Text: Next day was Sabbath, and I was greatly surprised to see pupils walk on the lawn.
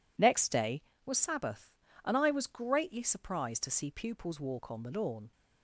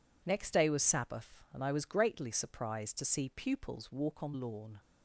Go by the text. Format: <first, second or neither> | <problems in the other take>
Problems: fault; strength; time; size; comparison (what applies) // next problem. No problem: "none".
first | skips "the"; at 4.3 s